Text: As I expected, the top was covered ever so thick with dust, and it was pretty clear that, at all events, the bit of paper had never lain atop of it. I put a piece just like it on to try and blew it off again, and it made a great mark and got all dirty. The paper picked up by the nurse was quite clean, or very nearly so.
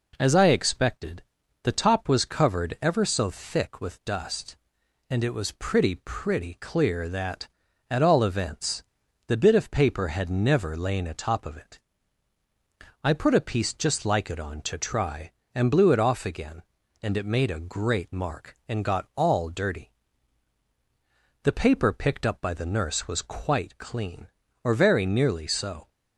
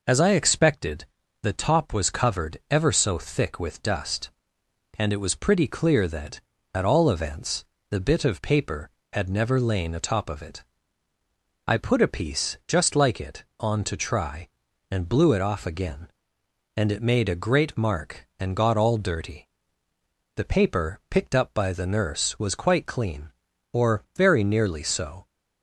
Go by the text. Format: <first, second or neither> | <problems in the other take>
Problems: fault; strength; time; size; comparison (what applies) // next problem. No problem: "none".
second | says "pretty" twice; at 6.0 s